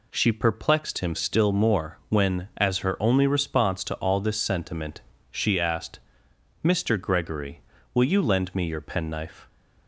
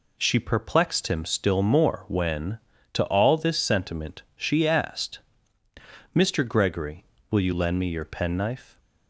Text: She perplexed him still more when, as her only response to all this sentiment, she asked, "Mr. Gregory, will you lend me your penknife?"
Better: first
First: none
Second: skips "as her only response"; at 2.7 s

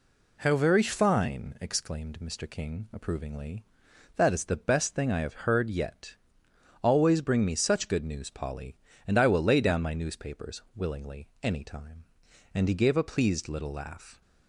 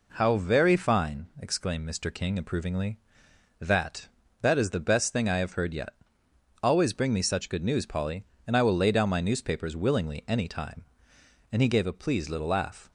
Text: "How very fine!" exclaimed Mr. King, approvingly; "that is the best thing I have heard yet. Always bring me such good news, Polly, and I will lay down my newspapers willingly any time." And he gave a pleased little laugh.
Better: first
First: none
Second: says "that" twice; at 4.4 s

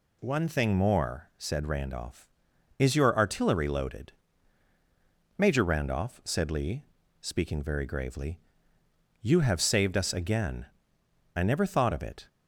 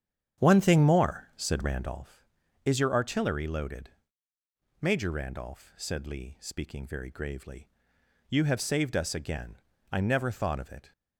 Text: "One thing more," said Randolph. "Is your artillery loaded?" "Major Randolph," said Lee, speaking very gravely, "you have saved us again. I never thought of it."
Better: first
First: none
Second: starts louder than the rest; strong; until 2.1 s; 8.5 dB

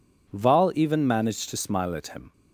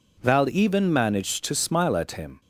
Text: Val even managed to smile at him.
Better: neither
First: none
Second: none

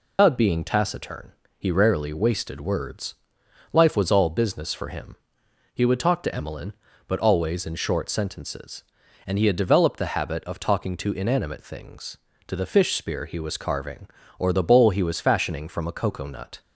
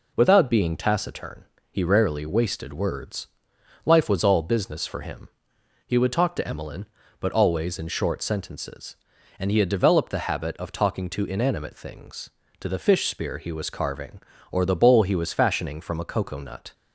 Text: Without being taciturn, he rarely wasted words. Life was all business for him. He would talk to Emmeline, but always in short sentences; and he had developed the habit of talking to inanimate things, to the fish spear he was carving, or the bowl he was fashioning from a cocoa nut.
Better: second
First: loses the start of "Without"; at 0.1 s; 170 ms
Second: none

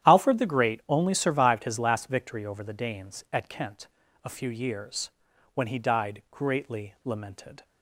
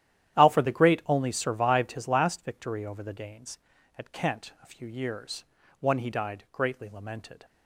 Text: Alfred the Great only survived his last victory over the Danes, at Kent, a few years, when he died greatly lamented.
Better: first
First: starts louder than the rest; strong; until 1.1 s; 11 dB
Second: starts louder than the rest; strong; until 1.4 s; 11.5 dB // says "one" for "when"; at 5.7 s

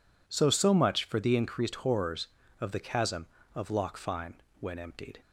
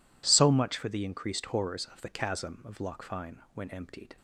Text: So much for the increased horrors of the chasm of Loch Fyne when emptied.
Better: second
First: says "So" twice; at 0.4 s // pauses between "Fyne" and "when"; slight; at 4.4 s; 0.20 s long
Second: none

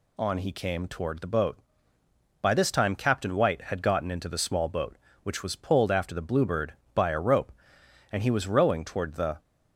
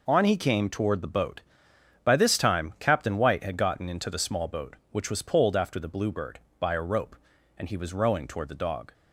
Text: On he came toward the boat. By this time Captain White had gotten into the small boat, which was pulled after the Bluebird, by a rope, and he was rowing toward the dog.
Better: second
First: stops before "dog"; at 9.3 s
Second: none

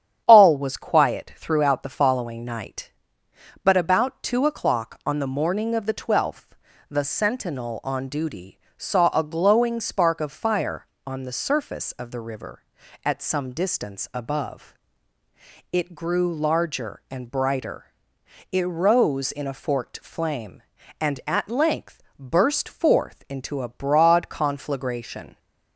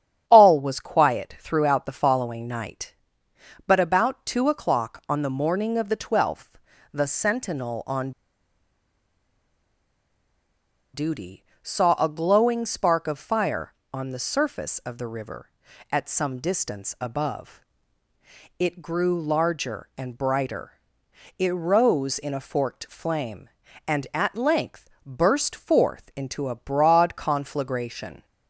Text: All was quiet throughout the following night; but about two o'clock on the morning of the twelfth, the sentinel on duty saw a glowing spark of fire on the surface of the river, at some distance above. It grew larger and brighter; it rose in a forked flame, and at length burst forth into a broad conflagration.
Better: first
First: starts louder than the rest; strong; until 1.2 s; 9 dB // pauses between "duty" and "saw"; slight; at 8.5 s; 0.18 s long // pauses between "length" and "burst"; slight; at 22.0 s; 0.16 s long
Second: starts louder than the rest; strong; until 1.2 s; 9 dB // pauses between "on" and "duty"; strong; at 8.1 s; 2.8 s long // pauses between "duty" and "saw"; slight; at 11.4 s; 0.18 s long // pauses between "length" and "burst"; slight; at 24.8 s; 0.16 s long

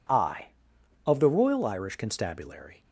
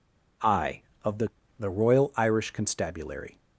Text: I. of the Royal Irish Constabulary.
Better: first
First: none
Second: says "the" twice; at 1.5 s

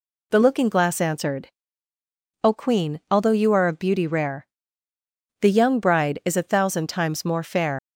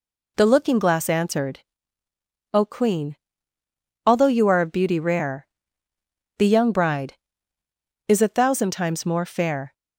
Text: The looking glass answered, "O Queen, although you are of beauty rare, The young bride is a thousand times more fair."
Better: second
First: leaves "fair" unfinished; at 7.7 s; 110 ms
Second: none

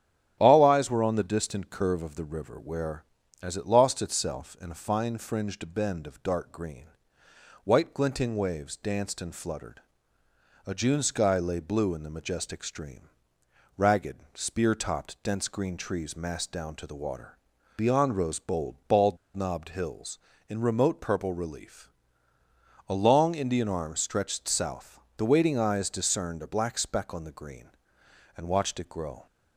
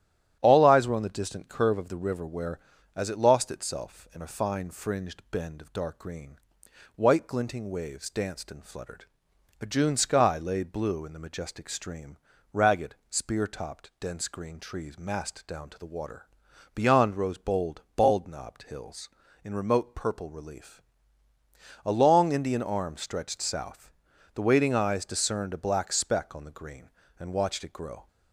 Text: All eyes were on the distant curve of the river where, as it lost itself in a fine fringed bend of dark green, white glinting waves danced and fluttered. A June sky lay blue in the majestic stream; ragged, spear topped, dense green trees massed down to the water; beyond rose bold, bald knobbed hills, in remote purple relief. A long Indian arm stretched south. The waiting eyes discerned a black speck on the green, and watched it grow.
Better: second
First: starts louder than the rest; strong; until 1.3 s; 10.5 dB // pauses between "bald" and "knobbed"; slight; at 19.1 s; 0.18 s long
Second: starts louder than the rest; strong; until 1.4 s; 11 dB

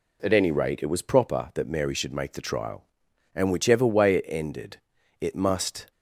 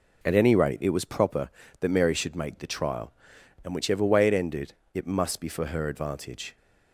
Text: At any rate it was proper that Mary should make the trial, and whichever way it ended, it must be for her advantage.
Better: second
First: stops before "be for her advantage"; at 5.9 s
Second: none

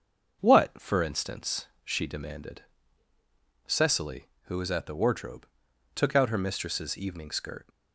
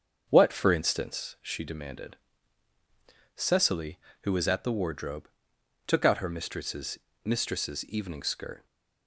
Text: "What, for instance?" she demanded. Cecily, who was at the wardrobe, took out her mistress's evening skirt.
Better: first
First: starts louder than the rest; until 1.4 s; 6.5 dB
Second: starts louder than the rest; until 1.3 s; 7 dB // says "mistress's" twice; at 7.2 s

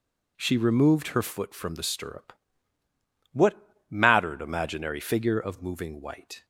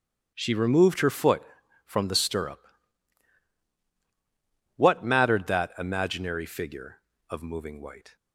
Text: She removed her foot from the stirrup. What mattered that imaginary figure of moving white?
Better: second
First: pauses between "What" and "mattered"; slight; at 3.5 s; 0.34 s long // skips "that"; at 4.4 s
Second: none

